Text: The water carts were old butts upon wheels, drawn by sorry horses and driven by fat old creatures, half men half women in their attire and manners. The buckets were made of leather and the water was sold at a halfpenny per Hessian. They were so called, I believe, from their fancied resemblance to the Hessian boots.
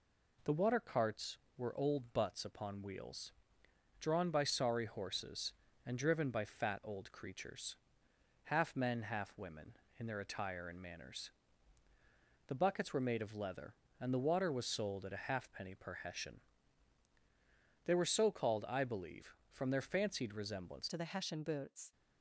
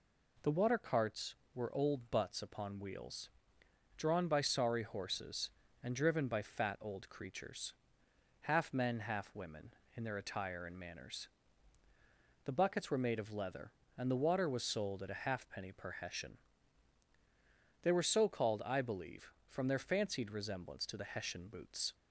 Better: second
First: changes voice at "to"; from 20.8 s on; 1.1 s long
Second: none

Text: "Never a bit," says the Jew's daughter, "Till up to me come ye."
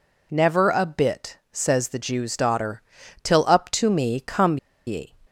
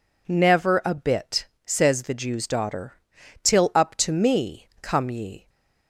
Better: second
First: pauses between "come" and "ye"; slight; at 4.5 s; 0.29 s long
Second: none

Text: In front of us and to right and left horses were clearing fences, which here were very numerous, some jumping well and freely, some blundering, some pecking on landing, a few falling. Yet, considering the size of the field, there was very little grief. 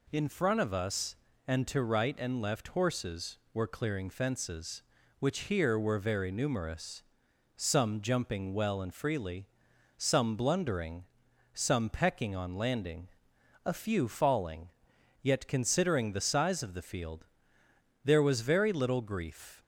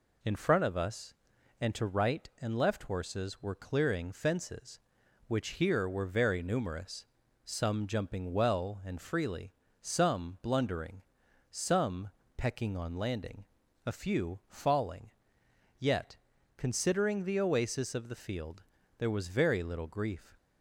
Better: first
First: none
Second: pauses between "some" and "pecking"; slight; at 12.0 s; 0.28 s long // says "oasis" for "size"; at 17.3 s

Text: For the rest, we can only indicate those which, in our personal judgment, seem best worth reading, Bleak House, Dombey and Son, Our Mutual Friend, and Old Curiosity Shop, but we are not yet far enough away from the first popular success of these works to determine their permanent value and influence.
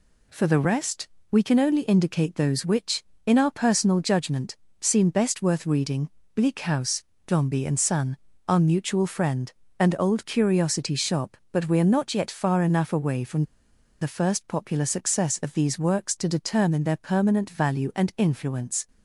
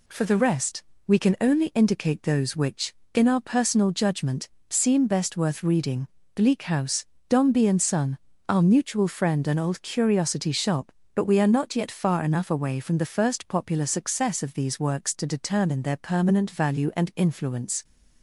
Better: second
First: pauses between "from" and "the"; noticeable; at 13.4 s; 0.57 s long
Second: none

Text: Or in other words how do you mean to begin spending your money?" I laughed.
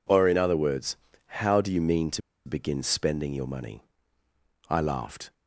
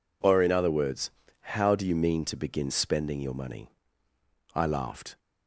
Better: second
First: pauses between "words" and "how"; noticeable; at 0.9 s; 0.46 s long // pauses between "to" and "begin"; slight; at 2.2 s; 0.25 s long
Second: pauses between "words" and "how"; noticeable; at 1.0 s; 0.46 s long

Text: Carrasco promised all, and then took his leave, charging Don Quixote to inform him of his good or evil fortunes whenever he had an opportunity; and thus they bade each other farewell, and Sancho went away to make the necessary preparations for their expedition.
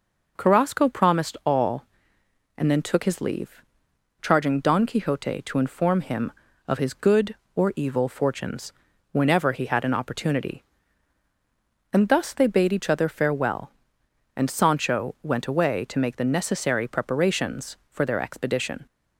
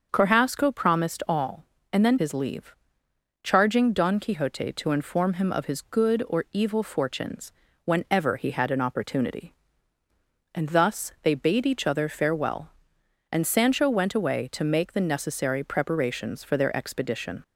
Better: first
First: pauses between "fortunes" and "whenever"; at 8.7 s; 0.38 s long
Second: starts louder than the rest; until 1.1 s; 7 dB // skips "took"; at 2.1 s // pauses between "fortunes" and "whenever"; slight; at 7.5 s; 0.34 s long

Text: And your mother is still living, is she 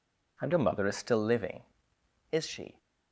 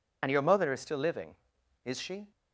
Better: first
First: none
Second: loses the start of "And"; at 0.2 s; 30 ms

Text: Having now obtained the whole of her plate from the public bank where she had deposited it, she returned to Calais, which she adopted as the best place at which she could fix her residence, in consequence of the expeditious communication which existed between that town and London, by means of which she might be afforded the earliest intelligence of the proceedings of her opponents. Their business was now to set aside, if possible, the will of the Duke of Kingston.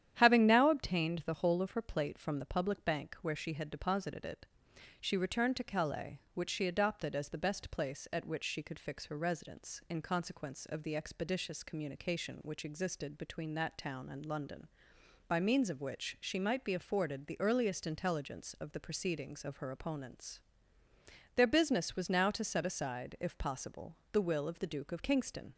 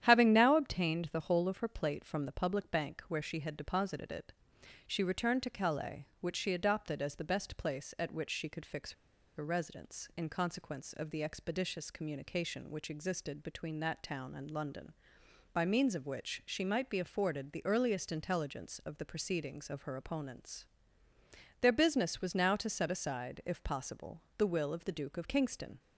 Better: first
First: starts louder than the rest; strong; until 1.1 s; 10 dB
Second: starts louder than the rest; strong; until 1.0 s; 10 dB // pauses between "fix" and "her"; at 8.9 s; 0.44 s long

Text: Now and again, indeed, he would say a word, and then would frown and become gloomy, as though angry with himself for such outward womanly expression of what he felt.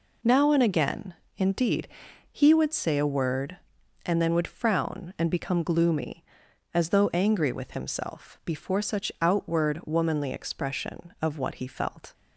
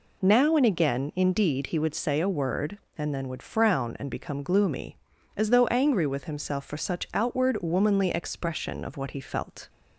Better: second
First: says "before" for "for"; at 8.4 s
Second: none

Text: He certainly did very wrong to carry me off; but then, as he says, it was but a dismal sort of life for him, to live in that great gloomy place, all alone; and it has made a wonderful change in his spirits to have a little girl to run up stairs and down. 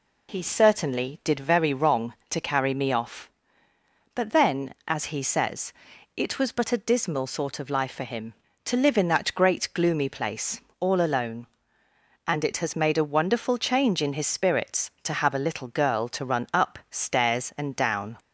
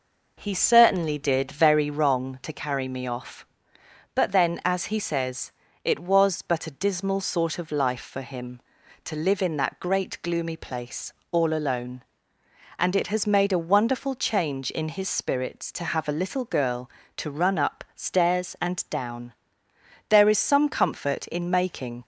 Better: first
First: none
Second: goes on to say "There is some comfort in making"; strong; from 20.0 s on; 1.9 s long

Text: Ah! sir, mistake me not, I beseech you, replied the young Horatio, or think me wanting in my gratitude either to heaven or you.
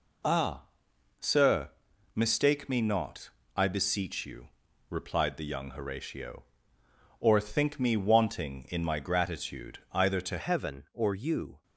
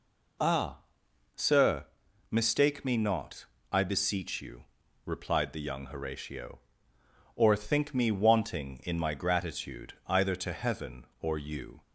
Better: second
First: changes voice at "heaven"; from 10.3 s on; 1.3 s long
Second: none

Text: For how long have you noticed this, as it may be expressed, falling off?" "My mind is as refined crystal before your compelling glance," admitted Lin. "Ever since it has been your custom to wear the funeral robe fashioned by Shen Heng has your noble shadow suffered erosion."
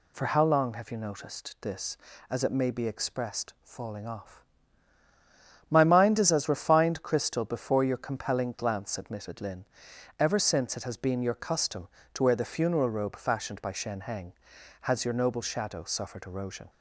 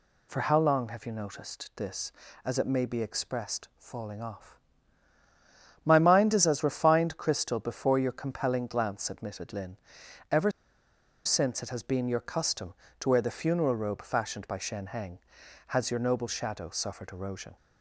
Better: first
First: none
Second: pauses between "Ever" and "since"; noticeable; at 10.5 s; 0.74 s long

